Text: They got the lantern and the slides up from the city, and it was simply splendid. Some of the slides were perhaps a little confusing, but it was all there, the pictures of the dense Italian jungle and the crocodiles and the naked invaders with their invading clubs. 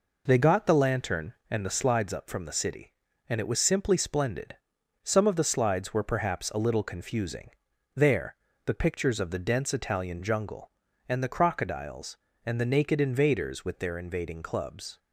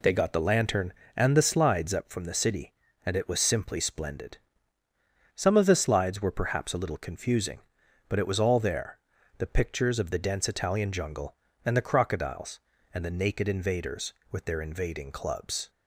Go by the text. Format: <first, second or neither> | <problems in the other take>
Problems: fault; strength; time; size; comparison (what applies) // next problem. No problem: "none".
second | skips "but it was all"; at 7.7 s